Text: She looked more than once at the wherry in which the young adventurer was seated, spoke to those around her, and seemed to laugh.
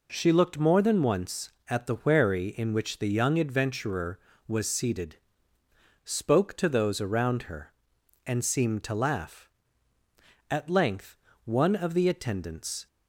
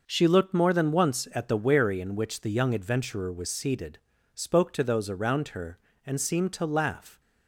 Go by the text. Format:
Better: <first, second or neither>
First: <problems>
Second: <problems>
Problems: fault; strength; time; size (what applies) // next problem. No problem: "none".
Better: second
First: goes on to say "At length one of the attendants"; strong; from 10.5 s on; 2.3 s long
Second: none